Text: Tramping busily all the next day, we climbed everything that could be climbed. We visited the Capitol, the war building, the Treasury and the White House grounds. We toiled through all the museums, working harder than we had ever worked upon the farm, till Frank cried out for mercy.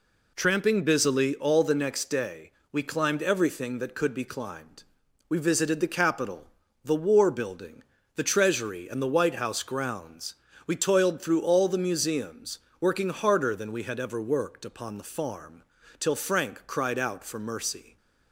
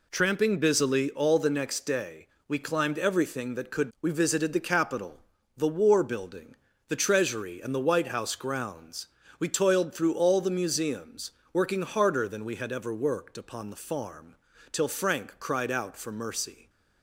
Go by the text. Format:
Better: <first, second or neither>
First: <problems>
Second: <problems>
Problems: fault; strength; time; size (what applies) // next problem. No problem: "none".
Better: first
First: none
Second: skips "be climbed"; at 3.9 s